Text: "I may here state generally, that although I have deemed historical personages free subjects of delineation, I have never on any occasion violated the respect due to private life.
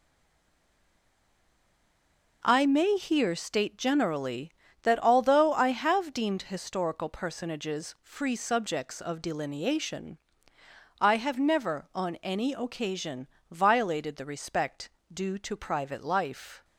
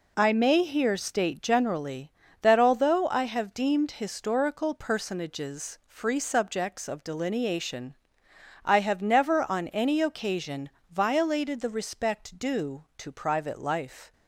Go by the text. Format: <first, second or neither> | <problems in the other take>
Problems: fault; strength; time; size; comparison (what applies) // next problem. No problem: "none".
second | stays silent before the first word; until 2.4 s; 2.4 s long // pauses between "occasion" and "violated"; slight; at 13.2 s; 0.22 s long; slight in the second // pauses between "respect" and "due"; slight; at 14.8 s; 0.24 s long